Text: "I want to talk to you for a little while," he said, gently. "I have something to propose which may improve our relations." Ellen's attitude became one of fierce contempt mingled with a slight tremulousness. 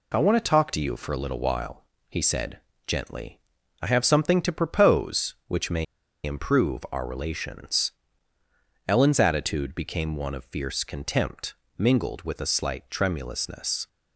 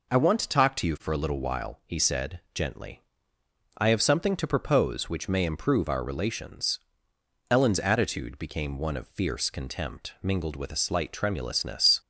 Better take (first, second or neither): second